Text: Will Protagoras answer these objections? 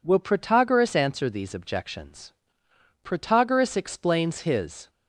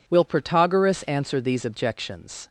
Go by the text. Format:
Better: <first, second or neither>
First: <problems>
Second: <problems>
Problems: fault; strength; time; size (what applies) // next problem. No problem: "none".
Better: second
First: goes on to say "Protagoras explains his"; strong; from 3.0 s on; 1.8 s long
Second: none